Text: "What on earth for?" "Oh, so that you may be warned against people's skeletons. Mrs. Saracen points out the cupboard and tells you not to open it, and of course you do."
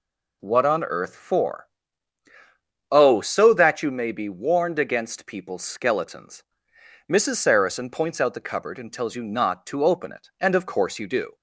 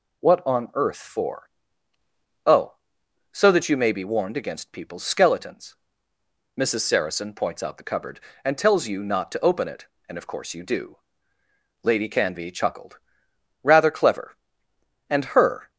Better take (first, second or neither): first